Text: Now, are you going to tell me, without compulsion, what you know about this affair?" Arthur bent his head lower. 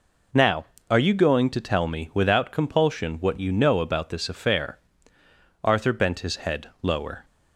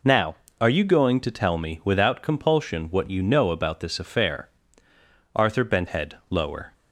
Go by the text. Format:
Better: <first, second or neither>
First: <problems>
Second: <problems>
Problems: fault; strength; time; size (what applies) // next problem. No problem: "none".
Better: first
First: none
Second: skips "his"; at 5.8 s